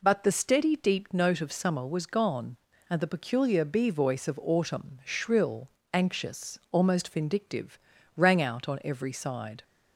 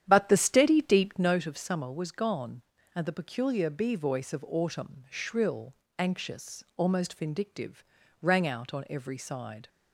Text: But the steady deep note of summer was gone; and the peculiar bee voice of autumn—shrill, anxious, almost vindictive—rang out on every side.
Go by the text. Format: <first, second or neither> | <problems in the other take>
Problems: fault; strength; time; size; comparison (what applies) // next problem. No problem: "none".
first | starts louder than the rest; strong; until 1.4 s; 10 dB